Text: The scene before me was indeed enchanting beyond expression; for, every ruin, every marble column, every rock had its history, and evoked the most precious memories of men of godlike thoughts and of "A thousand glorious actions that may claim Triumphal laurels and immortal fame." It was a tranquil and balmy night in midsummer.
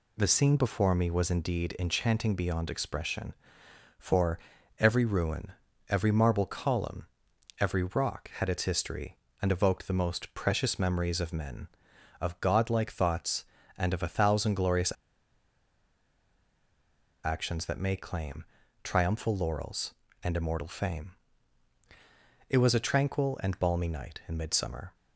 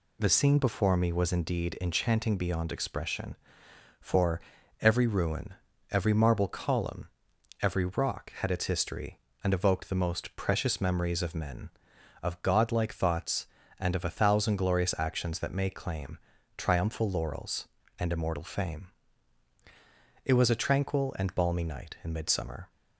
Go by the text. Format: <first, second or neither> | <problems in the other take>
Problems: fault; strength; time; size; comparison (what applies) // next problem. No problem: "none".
second | pauses between "glorious" and "actions"; strong; at 14.9 s; 2.3 s long // pauses between "claim" and "Triumphal"; at 18.4 s; 0.38 s long; also in the second